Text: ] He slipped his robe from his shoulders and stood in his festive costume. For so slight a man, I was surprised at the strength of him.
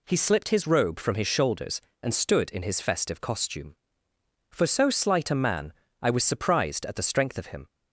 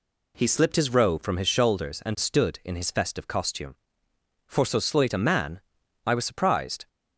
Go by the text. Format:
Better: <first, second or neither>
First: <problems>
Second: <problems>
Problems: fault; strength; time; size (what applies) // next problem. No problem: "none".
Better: first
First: none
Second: stops before "at the strength of him"; at 6.8 s